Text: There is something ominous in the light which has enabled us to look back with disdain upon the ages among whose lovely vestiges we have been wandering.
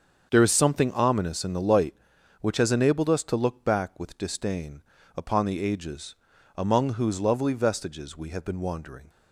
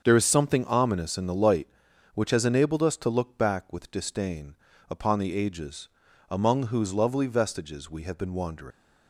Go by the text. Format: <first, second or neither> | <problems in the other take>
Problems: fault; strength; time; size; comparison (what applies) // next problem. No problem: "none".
first | starts louder than the rest; until 1.0 s; 7 dB; also in the first // pauses between "disdain" and "upon"; slight; at 4.5 s; 0.36 s long; slight in the first // pauses between "ages" and "among"; at 5.8 s; 0.42 s long; also in the first // leaves "wandering" unfinished; at 8.7 s; 120 ms